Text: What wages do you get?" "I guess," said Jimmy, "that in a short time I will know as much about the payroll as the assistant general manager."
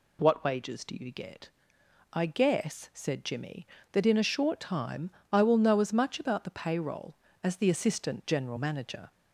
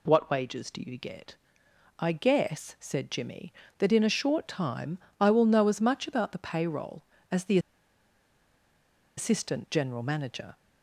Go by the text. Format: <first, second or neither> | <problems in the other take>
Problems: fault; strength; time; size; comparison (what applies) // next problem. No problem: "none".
first | pauses between "time" and "I"; slight; at 4.9 s; 0.22 s long; slight in the first // pauses between "the" and "assistant"; strong; at 7.5 s; 1.5 s long